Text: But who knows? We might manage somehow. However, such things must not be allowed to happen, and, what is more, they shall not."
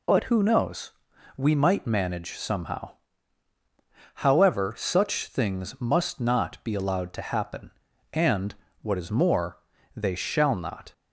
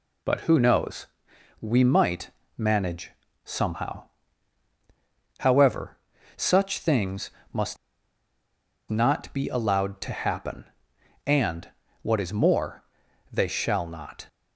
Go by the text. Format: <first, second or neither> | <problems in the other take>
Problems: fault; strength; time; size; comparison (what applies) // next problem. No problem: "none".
first | pauses between "might" and "manage"; slight; at 2.3 s; 0.26 s long // pauses between "manage" and "somehow"; slight; at 3.1 s; 0.34 s long // pauses between "things" and "must"; slight; at 7.3 s; 0.20 s long // pauses between "must" and "not"; at 7.7 s; 1.1 s long